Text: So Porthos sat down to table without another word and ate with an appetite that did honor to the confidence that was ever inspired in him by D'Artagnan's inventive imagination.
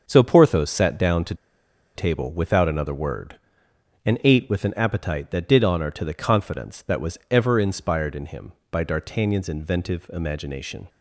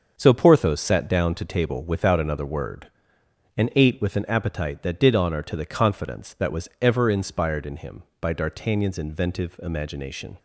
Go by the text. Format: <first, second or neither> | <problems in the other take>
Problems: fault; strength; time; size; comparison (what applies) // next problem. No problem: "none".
second | starts louder than the rest; until 1.0 s; 6.5 dB; also in the second // pauses between "to" and "table"; noticeable; at 1.3 s; 0.61 s long